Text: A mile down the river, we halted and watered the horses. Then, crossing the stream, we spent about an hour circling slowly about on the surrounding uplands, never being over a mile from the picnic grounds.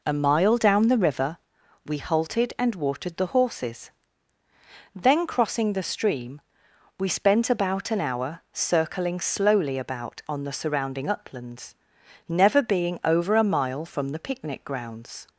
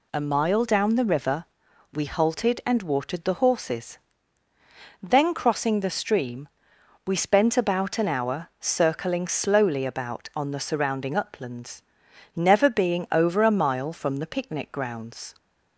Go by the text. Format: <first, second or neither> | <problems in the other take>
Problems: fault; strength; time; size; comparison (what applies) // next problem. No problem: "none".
second | starts louder than the rest; noticeable; until 1.3 s; 4 dB